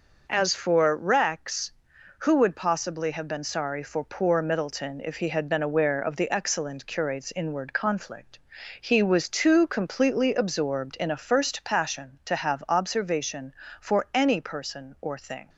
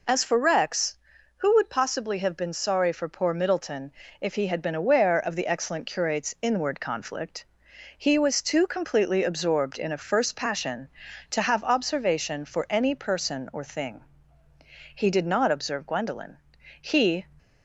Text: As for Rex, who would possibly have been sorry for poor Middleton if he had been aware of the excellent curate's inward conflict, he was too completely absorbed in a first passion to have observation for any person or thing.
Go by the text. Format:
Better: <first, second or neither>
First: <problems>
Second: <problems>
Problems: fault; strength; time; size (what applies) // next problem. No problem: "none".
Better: first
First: none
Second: pauses between "Middleton" and "if"; slight; at 3.9 s; 0.28 s long // goes on to say "He did not observe Gwendolen he"; strong; from 14.9 s on; 2.2 s long